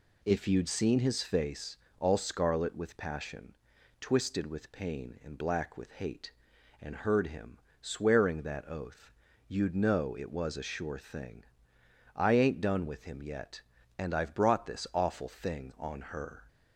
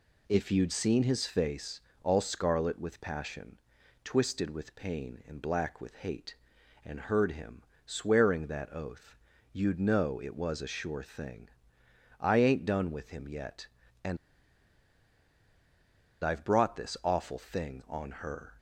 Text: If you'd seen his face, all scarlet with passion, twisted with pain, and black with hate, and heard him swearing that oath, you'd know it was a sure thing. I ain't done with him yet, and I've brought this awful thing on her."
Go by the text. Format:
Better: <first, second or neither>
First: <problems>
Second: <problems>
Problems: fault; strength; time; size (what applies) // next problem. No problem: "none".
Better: first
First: pauses between "him" and "swearing"; slight; at 7.5 s; 0.24 s long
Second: pauses between "him" and "swearing"; slight; at 7.6 s; 0.24 s long // pauses between "and" and "I've"; strong; at 14.1 s; 2.0 s long